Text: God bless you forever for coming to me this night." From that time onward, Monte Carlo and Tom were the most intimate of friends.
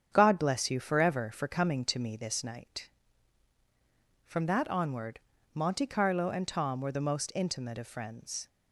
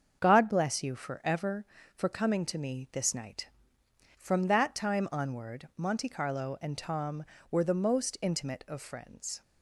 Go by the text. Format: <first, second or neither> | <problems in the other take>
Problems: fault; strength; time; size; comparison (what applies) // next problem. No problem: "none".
second | starts louder than the rest; strong; until 1.1 s; 8 dB; also in the second // skips "time"; at 4.6 s